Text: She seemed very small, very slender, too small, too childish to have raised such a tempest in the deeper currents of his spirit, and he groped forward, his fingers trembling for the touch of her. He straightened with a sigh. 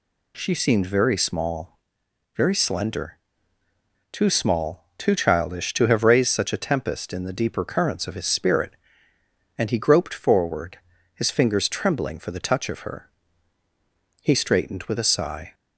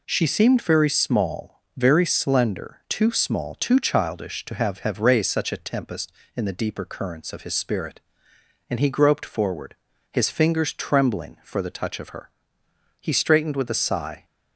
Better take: first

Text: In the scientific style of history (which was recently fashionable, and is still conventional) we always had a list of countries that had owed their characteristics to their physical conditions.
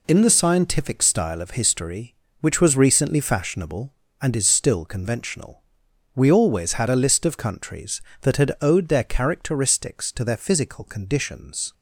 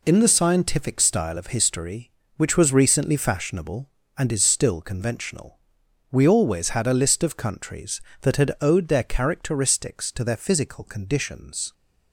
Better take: neither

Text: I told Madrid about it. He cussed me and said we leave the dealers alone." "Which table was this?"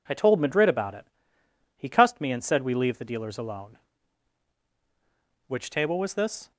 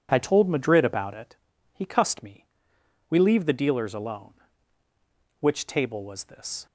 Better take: first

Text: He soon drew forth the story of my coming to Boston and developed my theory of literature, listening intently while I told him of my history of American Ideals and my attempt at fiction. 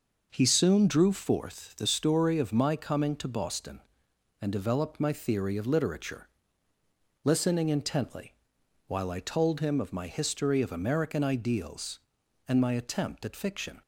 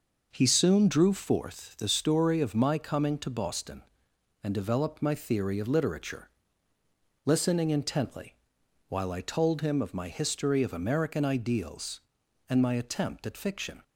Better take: neither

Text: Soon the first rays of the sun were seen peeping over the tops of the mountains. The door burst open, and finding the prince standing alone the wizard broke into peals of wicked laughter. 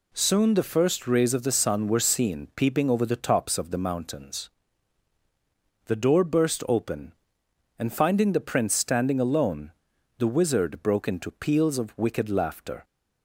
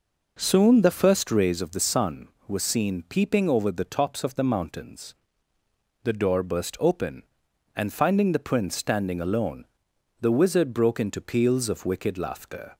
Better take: neither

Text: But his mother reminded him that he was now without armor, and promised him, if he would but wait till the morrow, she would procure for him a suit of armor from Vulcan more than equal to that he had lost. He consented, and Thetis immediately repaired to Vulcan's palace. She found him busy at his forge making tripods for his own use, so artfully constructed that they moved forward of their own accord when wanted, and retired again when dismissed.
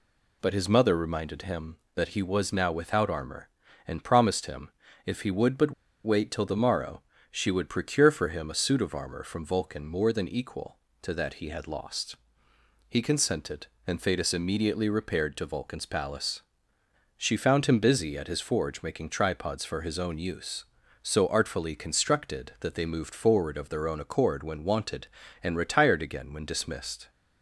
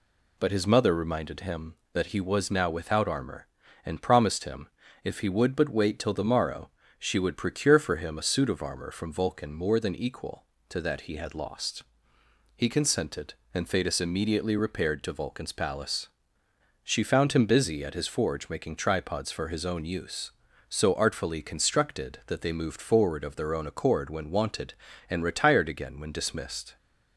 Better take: second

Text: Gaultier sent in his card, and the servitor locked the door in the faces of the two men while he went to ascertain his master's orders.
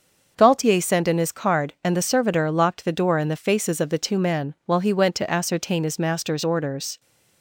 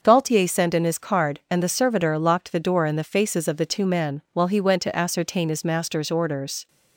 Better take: neither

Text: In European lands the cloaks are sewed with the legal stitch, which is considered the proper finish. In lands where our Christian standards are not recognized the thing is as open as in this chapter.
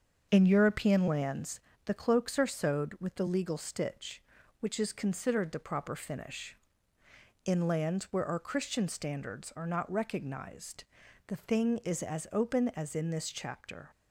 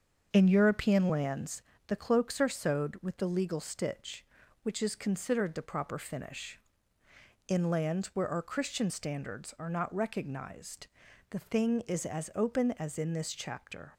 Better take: neither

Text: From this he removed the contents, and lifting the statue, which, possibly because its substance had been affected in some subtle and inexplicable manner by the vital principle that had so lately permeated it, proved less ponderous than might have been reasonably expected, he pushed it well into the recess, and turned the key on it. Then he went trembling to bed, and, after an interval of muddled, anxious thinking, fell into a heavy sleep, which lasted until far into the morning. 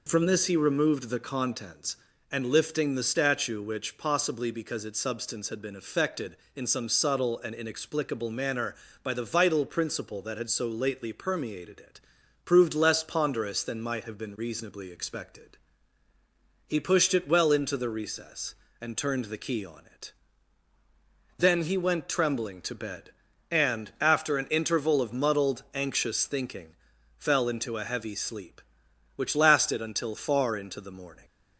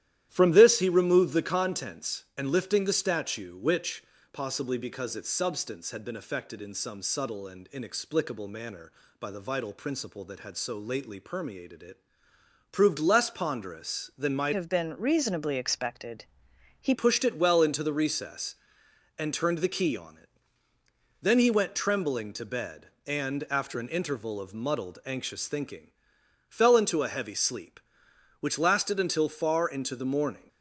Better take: first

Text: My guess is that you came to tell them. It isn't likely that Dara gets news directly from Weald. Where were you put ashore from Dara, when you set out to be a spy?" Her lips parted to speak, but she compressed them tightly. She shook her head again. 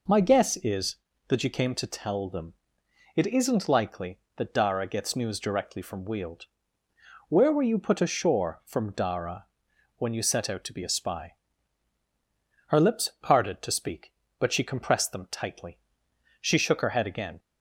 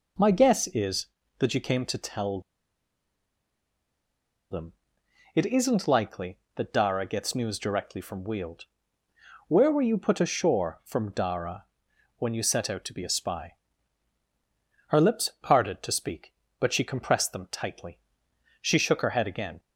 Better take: first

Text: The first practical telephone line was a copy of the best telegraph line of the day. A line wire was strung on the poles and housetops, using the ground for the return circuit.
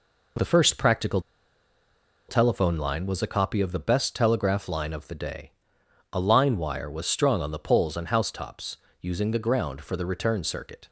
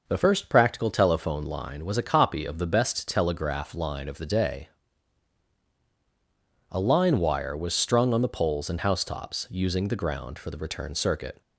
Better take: second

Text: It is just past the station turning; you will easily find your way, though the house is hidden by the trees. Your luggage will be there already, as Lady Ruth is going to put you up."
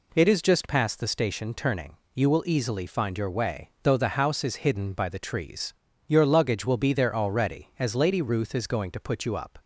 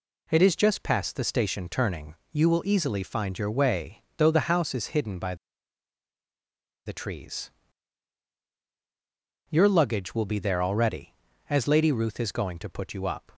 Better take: first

